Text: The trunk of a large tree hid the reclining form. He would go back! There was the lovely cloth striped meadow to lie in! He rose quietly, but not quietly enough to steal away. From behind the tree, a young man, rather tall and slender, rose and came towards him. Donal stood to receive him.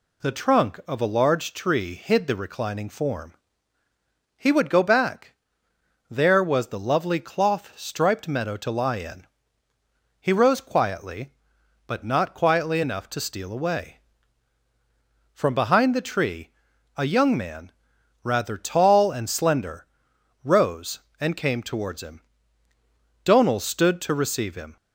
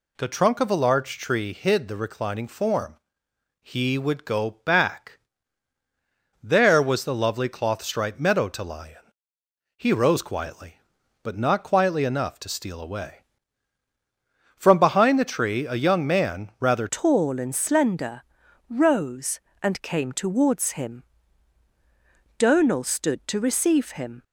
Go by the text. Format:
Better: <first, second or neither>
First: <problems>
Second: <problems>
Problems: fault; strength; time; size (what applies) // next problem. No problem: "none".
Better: first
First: none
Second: changes voice at "tall"; from 16.9 s on; 7.3 s long